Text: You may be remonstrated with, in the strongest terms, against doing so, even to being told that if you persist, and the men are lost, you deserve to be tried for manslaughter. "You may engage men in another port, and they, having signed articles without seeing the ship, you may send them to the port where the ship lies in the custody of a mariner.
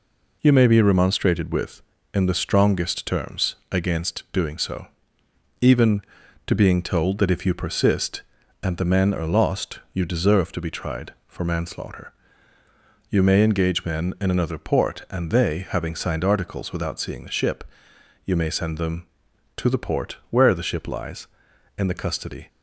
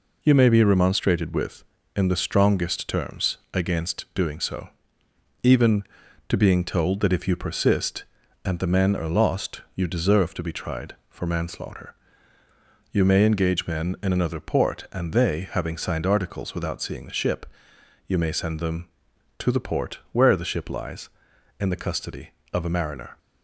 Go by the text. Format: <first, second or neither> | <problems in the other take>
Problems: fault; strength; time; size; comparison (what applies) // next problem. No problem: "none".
second | stops before "of a mariner"; at 22.4 s